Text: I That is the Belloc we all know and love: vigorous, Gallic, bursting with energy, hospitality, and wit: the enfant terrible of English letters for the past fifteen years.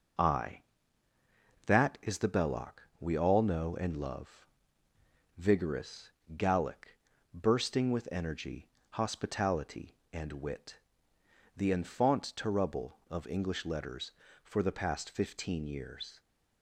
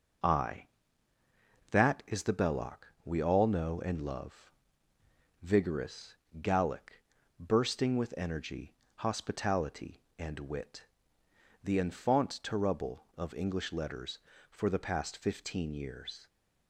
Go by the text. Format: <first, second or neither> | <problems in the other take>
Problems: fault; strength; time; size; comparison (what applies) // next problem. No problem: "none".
neither | pauses between "Belloc" and "we"; slight; the same in both